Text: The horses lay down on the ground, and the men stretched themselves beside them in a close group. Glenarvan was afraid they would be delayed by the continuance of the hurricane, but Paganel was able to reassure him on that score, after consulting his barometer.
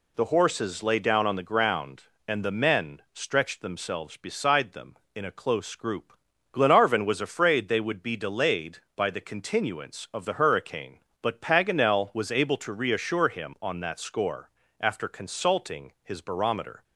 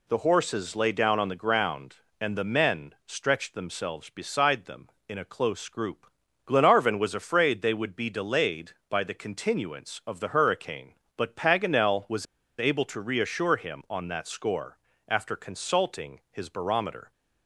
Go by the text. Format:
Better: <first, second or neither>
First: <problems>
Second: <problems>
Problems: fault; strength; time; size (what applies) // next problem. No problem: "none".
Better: first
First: none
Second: pauses between "was" and "able"; slight; at 12.2 s; 0.34 s long